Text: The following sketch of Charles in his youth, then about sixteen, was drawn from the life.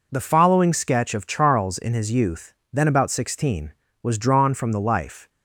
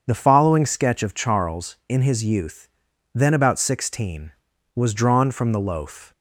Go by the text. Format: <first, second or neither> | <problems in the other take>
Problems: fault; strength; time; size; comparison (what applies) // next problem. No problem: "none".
first | starts louder than the rest; until 1.0 s; 7 dB // says "loaf" for "life"; at 5.5 s